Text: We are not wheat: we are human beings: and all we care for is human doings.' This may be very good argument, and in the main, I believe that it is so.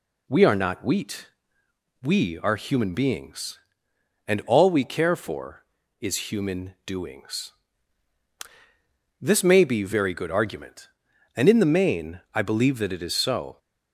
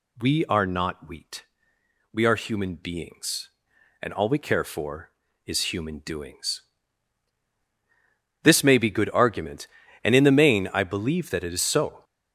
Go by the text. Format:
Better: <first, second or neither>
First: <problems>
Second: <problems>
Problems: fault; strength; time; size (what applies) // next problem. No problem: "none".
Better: first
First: none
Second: skips "very"; at 8.8 s